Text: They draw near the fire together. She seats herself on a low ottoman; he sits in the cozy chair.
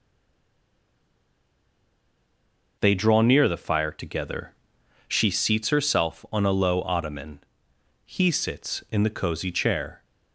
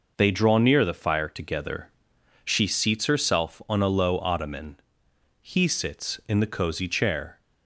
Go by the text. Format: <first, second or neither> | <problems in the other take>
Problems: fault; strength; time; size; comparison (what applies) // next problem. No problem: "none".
second | stays silent before the first word; strong; until 2.7 s; 2.7 s long